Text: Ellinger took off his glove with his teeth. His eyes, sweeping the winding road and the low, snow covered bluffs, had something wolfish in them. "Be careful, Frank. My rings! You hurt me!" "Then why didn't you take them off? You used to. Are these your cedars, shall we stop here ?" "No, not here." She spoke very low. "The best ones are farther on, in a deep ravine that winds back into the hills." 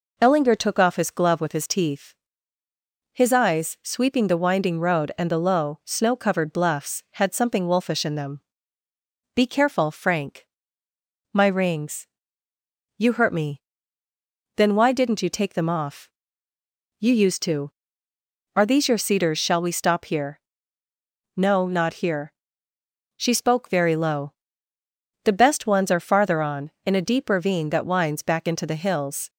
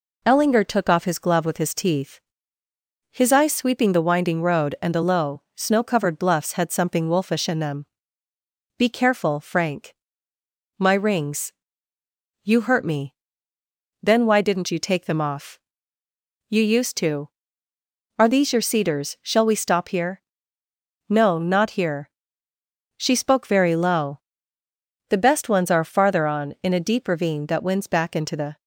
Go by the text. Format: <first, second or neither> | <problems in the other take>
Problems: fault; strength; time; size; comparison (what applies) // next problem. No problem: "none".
first | stops before "hills"; at 28.6 s